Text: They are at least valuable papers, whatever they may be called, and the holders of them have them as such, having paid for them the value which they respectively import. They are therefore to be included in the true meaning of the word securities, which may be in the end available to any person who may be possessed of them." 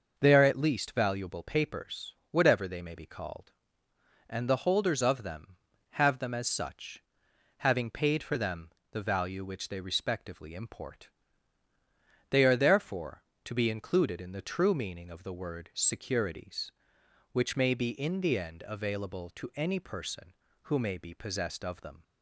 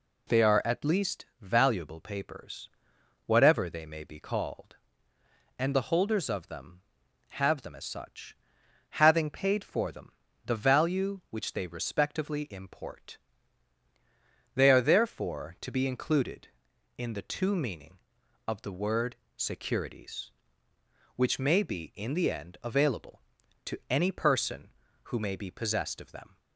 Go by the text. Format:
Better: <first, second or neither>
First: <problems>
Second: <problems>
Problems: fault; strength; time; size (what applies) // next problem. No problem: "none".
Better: first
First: pauses between "them" and "the"; slight; at 8.7 s; 0.22 s long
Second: pauses between "least" and "valuable"; slight; at 1.2 s; 0.16 s long // pauses between "them" and "the"; slight; at 10.1 s; 0.32 s long // says "two" for "true"; at 17.2 s // pauses between "word" and "securities"; slight; at 19.1 s; 0.20 s long